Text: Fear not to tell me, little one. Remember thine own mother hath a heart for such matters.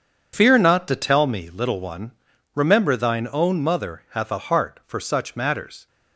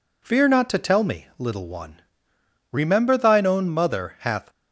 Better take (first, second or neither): first